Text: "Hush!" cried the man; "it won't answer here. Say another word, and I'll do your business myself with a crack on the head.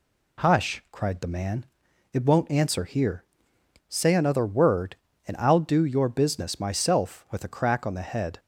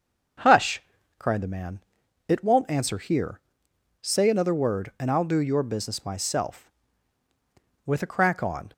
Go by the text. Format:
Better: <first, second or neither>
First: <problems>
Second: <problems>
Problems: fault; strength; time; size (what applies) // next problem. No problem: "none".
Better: first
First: none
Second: starts louder than the rest; until 1.8 s; 6.5 dB // stops before "the head"; at 8.7 s